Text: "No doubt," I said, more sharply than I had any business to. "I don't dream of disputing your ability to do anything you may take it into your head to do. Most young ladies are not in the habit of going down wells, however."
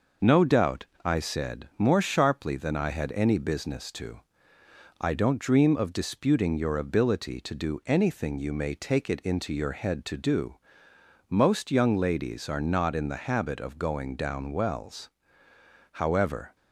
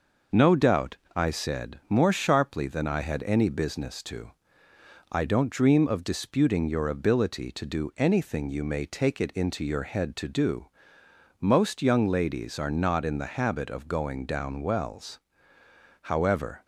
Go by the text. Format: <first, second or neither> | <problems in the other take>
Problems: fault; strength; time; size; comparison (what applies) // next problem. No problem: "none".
neither | none